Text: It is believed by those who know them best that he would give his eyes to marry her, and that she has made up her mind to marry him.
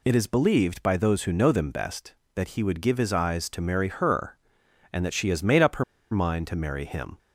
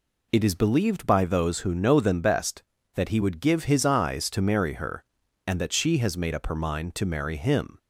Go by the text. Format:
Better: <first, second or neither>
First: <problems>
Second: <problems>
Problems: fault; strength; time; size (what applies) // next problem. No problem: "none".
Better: second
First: pauses between "her" and "mind"; slight; at 5.8 s; 0.28 s long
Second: none